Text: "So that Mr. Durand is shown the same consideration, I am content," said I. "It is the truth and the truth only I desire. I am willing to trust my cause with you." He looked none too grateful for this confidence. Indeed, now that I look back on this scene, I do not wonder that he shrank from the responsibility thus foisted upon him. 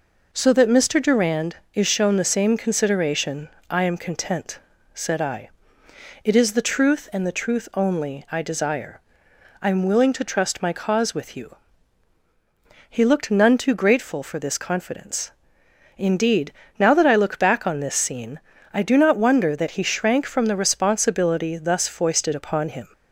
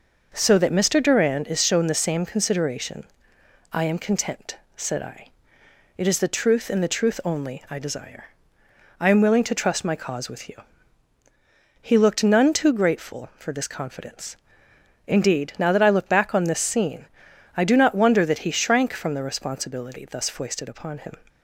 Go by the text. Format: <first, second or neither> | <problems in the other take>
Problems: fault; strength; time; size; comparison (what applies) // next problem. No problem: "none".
neither | none